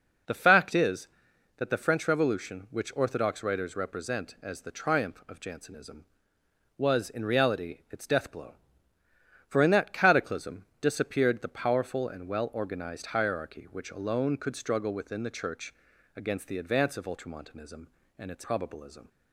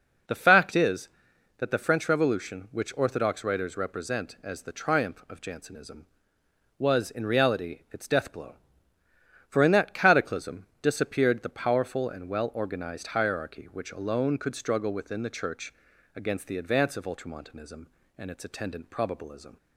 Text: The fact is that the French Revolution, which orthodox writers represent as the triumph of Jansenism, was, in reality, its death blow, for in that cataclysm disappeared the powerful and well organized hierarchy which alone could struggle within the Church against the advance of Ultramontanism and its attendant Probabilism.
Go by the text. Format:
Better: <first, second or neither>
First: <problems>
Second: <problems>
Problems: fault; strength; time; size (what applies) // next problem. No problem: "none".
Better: second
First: pauses between "Church" and "against"; at 15.7 s; 0.42 s long // skips "attendant"; at 18.4 s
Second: pauses between "Church" and "against"; at 15.7 s; 0.42 s long